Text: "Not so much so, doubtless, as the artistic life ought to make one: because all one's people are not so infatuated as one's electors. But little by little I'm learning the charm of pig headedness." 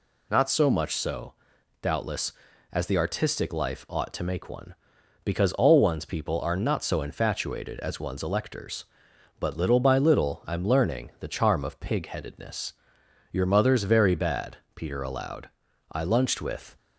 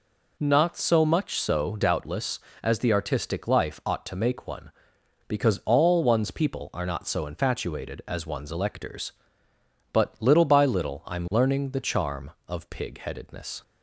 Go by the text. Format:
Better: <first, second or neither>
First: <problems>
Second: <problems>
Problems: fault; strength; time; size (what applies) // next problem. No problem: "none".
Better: second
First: goes on to say "Your mother's very bad Peter allowed I lunched with"; strong; from 13.3 s on; 3.4 s long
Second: none